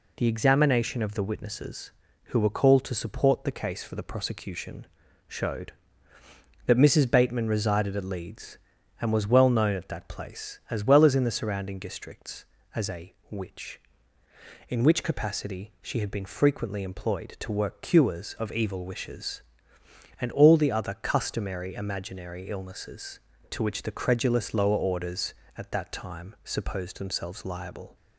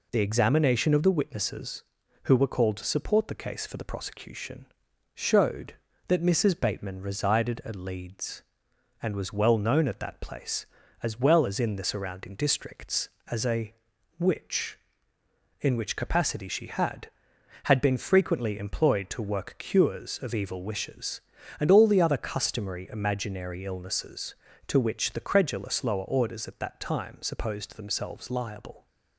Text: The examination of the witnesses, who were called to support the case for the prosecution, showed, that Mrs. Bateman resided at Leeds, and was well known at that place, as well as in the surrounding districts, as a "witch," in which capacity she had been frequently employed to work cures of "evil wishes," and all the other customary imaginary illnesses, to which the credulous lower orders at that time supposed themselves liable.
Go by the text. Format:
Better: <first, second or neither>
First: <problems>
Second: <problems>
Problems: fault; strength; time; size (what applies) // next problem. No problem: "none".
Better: first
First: pauses between "a" and "witch"; slight; at 13.1 s; 0.16 s long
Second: pauses between "a" and "witch"; at 13.7 s; 0.42 s long // says "had" twice; at 17.6 s